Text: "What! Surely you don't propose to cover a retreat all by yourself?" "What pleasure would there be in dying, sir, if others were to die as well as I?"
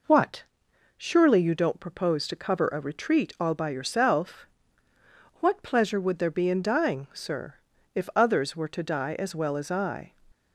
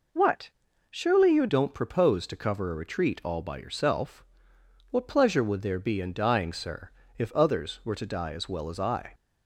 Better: first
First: none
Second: changes voice at "don't"; from 1.4 s on; 7.7 s long

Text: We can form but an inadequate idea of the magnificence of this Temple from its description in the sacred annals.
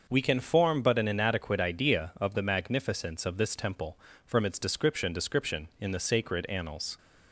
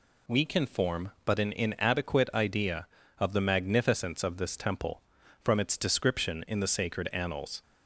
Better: second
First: starts louder than the rest; noticeable; until 1.1 s; 6 dB // says "description" twice; at 5.1 s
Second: none

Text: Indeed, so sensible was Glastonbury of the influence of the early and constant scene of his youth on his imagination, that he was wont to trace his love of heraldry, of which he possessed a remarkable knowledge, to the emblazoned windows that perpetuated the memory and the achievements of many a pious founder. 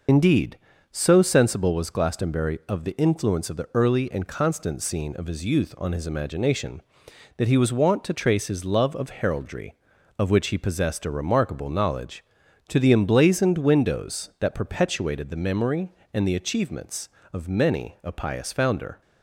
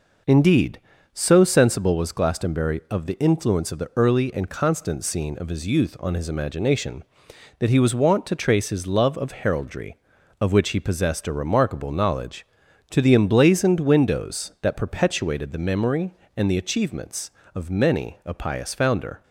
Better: second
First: loses the start of "Indeed"; at 0.0 s; 50 ms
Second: none

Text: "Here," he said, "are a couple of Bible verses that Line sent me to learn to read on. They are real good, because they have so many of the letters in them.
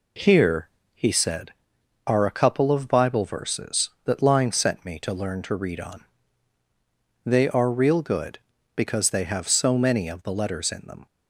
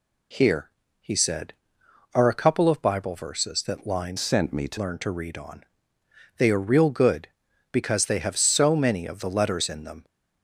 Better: first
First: none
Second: changes voice from "sent" to "to"; from 4.1 to 4.7 s; 0.6 s long

